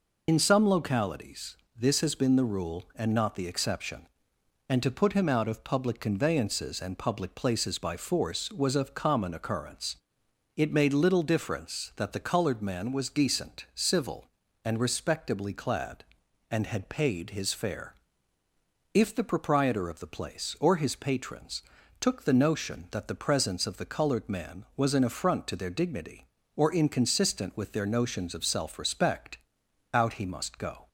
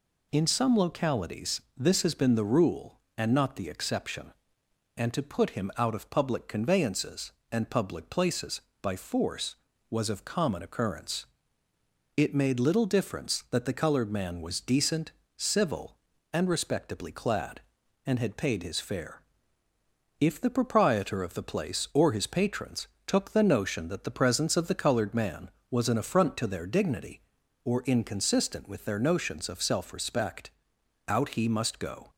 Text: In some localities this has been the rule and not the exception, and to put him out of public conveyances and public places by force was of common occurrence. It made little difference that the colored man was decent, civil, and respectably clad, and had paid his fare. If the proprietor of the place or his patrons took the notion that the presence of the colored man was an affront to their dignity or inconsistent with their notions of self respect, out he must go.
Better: second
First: loses the start of "In"; at 0.2 s; 45 ms // pauses between "localities" and "this"; slight; at 1.5 s; 0.22 s long // pauses between "patrons" and "took"; at 21.6 s; 0.38 s long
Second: pauses between "localities" and "this"; slight; at 1.6 s; 0.16 s long // pauses between "patrons" and "took"; slight; at 22.8 s; 0.18 s long

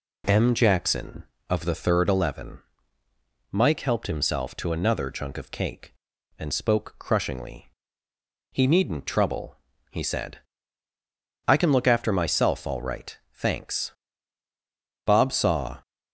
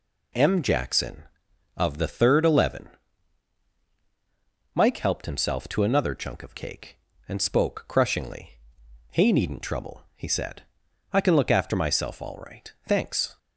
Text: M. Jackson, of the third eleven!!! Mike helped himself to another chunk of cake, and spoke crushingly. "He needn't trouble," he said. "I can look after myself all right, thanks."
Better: second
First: goes on to say "Bob saw"; noticeable; from 15.0 s on; 0.76 s long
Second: none

